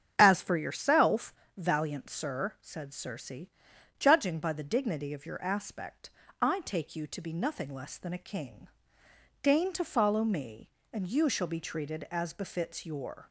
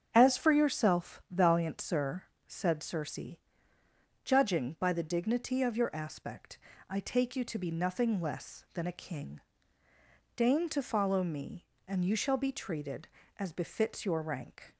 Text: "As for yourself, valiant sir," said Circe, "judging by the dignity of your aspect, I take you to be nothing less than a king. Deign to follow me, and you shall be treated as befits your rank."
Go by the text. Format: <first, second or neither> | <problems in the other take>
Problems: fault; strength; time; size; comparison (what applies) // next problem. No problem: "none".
second | starts louder than the rest; strong; until 1.2 s; 8 dB; strong in the second // stops before "rank"; at 13.2 s